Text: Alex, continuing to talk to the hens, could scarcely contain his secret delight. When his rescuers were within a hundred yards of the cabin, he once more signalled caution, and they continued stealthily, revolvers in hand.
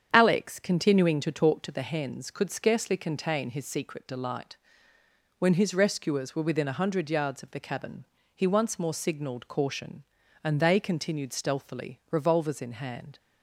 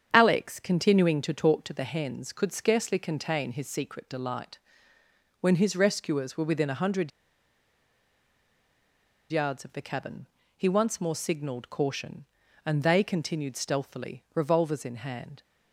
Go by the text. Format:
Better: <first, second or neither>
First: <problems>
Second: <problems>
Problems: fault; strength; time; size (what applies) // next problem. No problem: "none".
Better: first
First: starts louder than the rest; strong; until 1.1 s; 8 dB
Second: starts louder than the rest; strong; until 1.1 s; 8 dB // pauses between "hundred" and "yards"; strong; at 7.1 s; 2.2 s long